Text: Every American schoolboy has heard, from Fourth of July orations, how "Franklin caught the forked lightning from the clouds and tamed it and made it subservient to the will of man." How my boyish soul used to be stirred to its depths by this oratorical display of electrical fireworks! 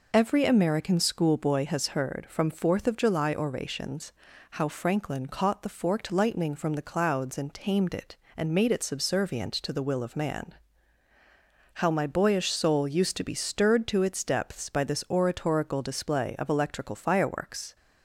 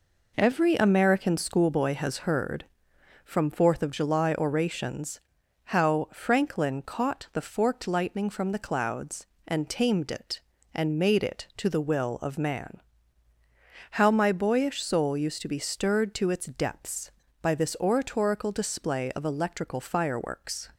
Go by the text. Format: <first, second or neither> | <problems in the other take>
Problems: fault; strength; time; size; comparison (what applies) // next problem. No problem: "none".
first | skips "subservient"; at 11.5 s